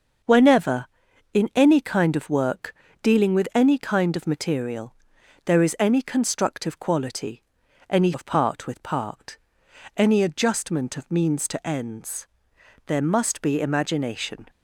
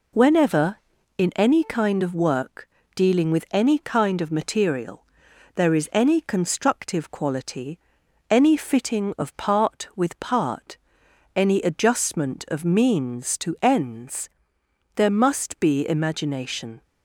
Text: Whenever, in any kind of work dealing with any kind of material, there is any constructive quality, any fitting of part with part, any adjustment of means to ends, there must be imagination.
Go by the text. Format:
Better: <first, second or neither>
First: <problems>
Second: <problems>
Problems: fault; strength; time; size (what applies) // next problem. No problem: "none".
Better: second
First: starts louder than the rest; until 1.7 s; 6.5 dB // pauses between "work" and "dealing"; slight; at 2.7 s; 0.30 s long // skips "fitting"; at 8.1 s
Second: pauses between "work" and "dealing"; slight; at 2.6 s; 0.26 s long